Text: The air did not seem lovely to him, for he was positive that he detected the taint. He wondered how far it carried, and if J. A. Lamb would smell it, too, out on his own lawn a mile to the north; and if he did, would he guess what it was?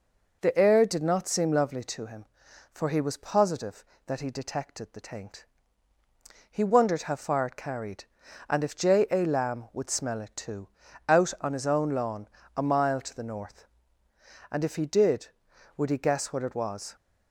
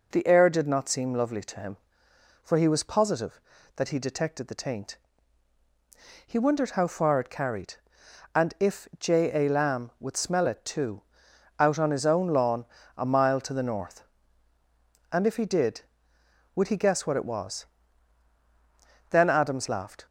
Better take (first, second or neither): first